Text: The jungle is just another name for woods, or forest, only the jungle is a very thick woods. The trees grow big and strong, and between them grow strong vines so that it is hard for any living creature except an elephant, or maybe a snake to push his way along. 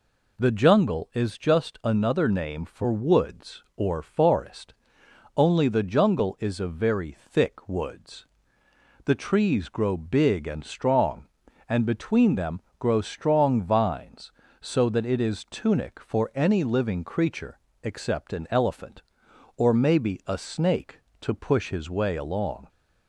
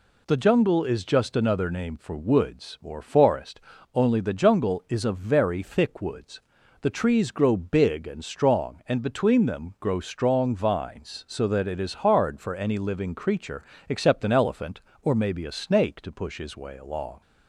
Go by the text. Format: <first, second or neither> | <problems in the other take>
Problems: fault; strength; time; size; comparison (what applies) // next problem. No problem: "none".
second | pauses between "them" and "grow"; slight; at 12.5 s; 0.20 s long // says "tunic" for "hard"; at 15.4 s // pauses between "creature" and "except"; slight; at 17.5 s; 0.24 s long; slight in the second